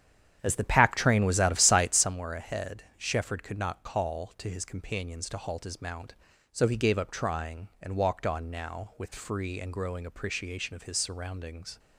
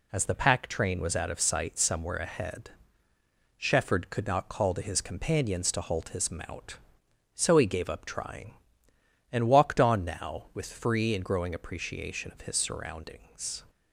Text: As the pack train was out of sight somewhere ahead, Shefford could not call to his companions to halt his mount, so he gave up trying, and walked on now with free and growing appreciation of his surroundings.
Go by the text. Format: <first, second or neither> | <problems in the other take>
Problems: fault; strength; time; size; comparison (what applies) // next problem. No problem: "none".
second | starts louder than the rest; strong; until 2.2 s; 9 dB